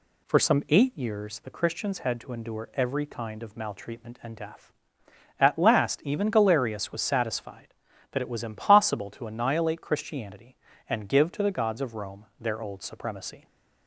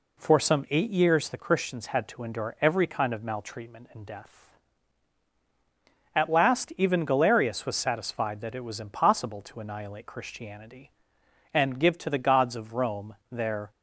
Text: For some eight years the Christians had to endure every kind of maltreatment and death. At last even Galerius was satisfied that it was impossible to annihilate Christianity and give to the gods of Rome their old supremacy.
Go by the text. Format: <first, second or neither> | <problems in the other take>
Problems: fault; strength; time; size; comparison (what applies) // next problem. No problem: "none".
first | pauses between "Rome" and "their"; slight; at 13.1 s; 0.16 s long // stops before "old supremacy"; at 13.7 s